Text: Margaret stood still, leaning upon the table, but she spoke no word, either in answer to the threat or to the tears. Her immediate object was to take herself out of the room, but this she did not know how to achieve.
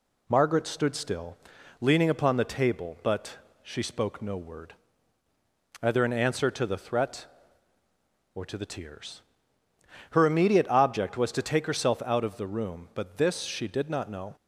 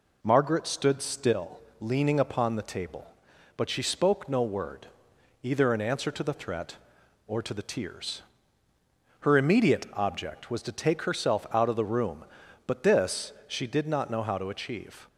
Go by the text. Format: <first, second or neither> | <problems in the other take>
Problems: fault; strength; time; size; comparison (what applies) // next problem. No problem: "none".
second | pauses between "but" and "she"; slight; at 3.3 s; 0.26 s long // stops before "how to achieve"; at 14.3 s